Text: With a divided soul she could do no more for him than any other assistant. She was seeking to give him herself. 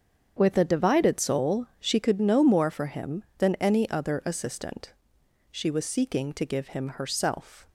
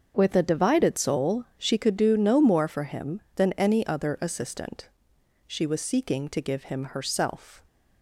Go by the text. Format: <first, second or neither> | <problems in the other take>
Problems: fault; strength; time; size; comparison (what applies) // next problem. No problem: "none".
second | starts louder than the rest; strong; until 1.3 s; 7.5 dB; also in the second // skips "do"; at 2.1 s